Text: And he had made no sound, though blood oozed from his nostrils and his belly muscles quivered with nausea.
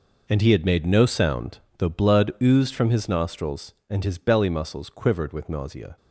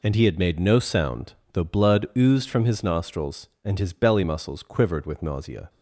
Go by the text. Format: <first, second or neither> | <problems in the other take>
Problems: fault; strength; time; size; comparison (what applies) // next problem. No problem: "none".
second | gets quieter; strong; throughout; 13.5 dB